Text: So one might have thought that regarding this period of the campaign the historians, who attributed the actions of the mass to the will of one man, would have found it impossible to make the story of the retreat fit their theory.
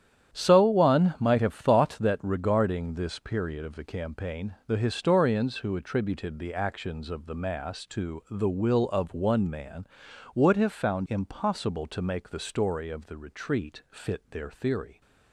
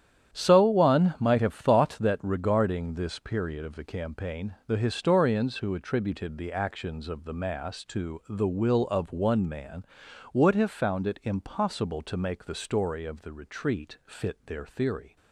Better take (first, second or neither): second